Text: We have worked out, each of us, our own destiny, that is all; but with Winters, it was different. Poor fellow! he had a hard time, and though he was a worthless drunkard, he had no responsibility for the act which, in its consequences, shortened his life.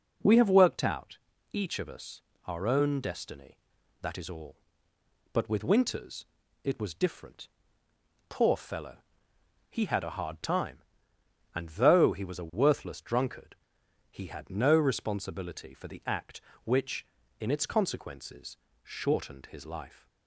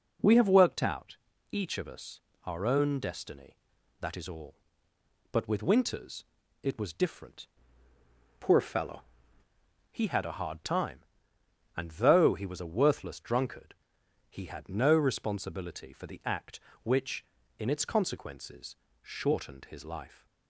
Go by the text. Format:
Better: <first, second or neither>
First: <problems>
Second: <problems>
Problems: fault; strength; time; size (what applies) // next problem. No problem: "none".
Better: first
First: none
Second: changes voice from "Poor" to "fellow"; from 8.3 to 9.0 s; 0.7 s long